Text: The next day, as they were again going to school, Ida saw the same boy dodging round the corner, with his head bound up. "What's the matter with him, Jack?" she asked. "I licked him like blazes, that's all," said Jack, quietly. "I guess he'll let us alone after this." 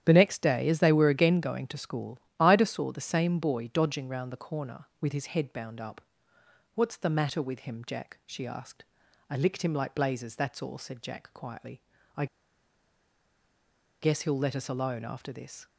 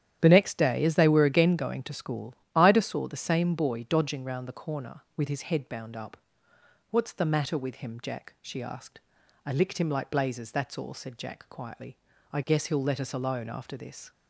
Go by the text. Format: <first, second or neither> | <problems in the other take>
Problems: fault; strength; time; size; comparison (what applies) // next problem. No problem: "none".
second | starts louder than the rest; strong; until 1.0 s; 10.5 dB; strong in the second // pauses between "I" and "guess"; strong; at 12.2 s; 1.7 s long